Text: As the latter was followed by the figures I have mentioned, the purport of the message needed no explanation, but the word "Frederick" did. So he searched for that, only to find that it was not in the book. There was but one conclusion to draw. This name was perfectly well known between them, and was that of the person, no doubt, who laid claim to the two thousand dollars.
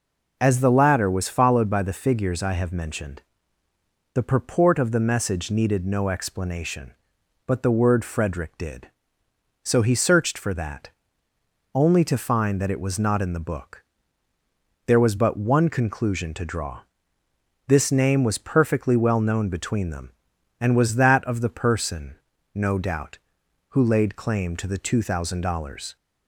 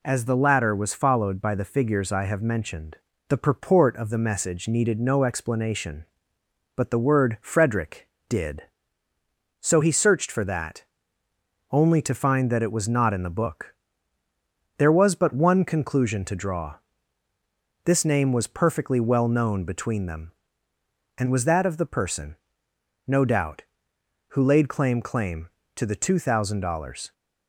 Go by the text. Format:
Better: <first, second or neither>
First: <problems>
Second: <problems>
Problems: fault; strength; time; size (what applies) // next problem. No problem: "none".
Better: first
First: none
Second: says "claim" twice; at 25.0 s